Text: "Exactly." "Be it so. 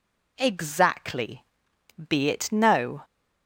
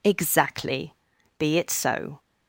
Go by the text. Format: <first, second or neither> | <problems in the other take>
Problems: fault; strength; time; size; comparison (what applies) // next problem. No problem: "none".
second | says "no" for "so"; at 2.5 s